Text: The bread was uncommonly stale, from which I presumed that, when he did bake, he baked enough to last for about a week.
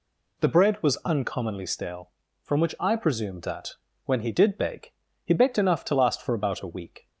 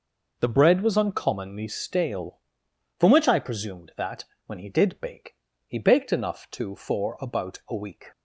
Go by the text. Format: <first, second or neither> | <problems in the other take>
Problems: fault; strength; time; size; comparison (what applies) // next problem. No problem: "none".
first | skips "last"; at 6.7 s